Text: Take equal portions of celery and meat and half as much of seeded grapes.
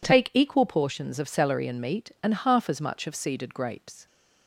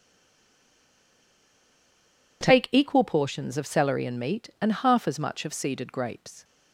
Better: first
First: none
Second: stays silent before the first word; until 2.4 s; 2.4 s long

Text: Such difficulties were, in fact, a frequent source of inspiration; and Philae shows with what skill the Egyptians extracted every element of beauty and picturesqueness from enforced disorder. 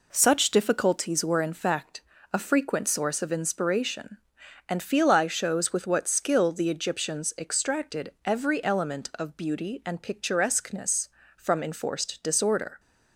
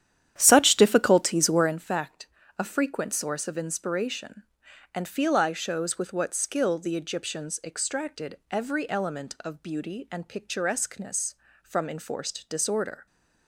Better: first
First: none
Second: starts louder than the rest; strong; until 1.8 s; 10.5 dB

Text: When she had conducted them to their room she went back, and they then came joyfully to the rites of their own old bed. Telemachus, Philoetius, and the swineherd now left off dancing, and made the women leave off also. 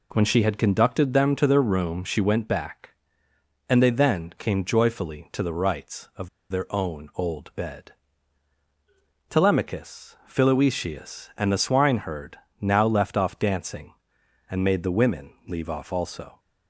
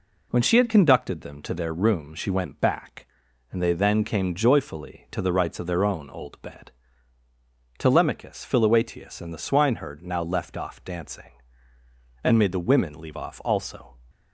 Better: second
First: pauses between "of" and "their"; slight; at 6.2 s; 0.22 s long // pauses between "swineherd" and "now"; slight; at 12.3 s; 0.24 s long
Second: none

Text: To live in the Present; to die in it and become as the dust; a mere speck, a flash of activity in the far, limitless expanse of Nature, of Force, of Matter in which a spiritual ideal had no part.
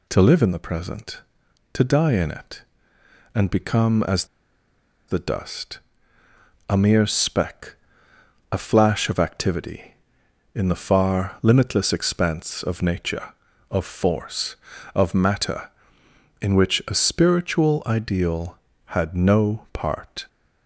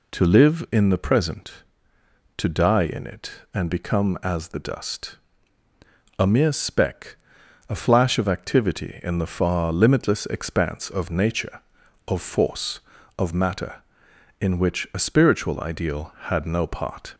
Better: second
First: pauses between "as" and "the"; noticeable; at 4.2 s; 0.82 s long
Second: none

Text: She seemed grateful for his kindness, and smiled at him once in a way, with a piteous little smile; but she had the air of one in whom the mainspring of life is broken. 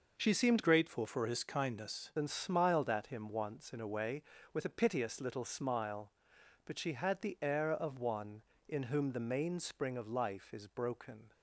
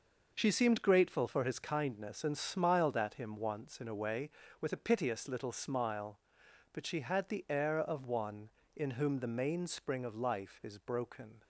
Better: second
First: changes voice from "grateful" to "kindness"; from 0.6 to 2.1 s; 1.5 s long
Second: none

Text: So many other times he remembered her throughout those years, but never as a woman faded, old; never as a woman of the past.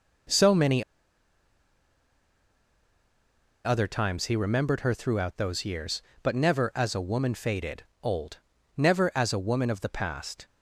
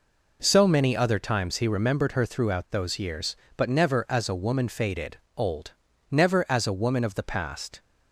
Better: second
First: pauses between "many" and "other"; strong; at 0.8 s; 2.8 s long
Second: none

